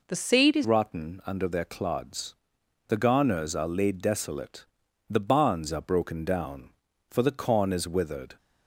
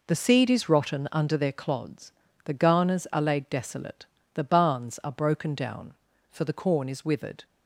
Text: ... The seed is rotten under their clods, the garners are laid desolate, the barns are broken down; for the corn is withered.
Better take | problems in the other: second | changes voice at "rotten"; from 0.6 s on; 7.7 s long

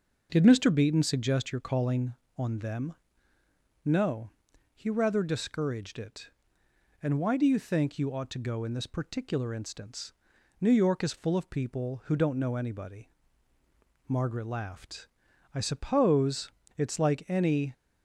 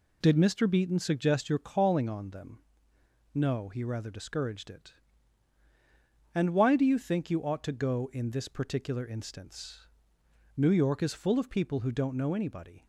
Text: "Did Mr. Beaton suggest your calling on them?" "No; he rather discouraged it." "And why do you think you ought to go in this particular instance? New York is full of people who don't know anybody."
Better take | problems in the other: second | goes on to say "Margaret laughed I suppose it's like any"; strong; from 14.0 s on; 3.6 s long

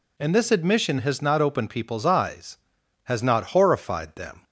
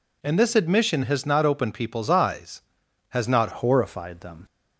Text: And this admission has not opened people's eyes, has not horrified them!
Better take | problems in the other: first | changes voice at "horrified"; from 3.5 s on; 0.9 s long

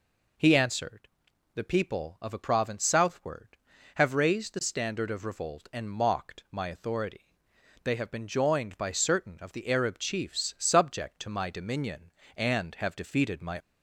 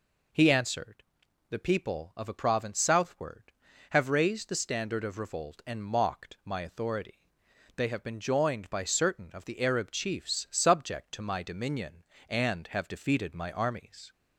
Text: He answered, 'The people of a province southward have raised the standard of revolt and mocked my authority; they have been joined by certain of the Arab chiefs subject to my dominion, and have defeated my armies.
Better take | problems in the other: second | stops before "armies"; at 13.5 s

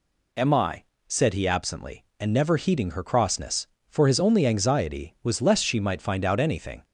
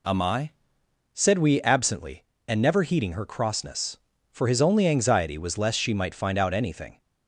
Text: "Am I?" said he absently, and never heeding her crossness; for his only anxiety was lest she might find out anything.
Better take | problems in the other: first | says "we" for "he"; at 1.3 s

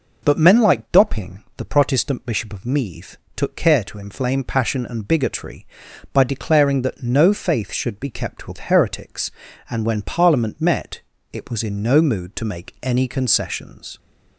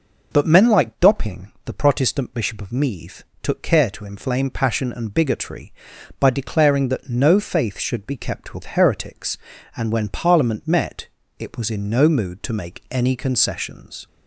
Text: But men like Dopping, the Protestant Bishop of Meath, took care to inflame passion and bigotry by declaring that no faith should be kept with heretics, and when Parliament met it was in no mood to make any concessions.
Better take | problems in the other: neither | pauses between "met" and "it"; slight; the same in both

